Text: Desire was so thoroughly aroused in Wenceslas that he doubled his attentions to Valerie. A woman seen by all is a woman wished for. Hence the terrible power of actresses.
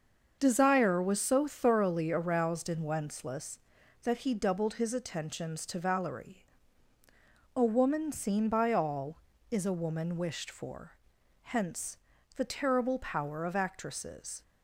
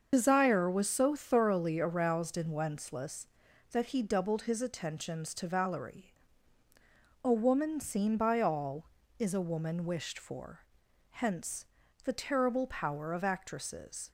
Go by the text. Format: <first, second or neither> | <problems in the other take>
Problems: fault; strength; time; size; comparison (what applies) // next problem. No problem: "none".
first | loses the start of "Desire"; at 0.1 s; 45 ms // starts louder than the rest; until 1.1 s; 6.5 dB; also in the first // pauses between "Hence" and "the"; at 11.6 s; 0.38 s long; also in the first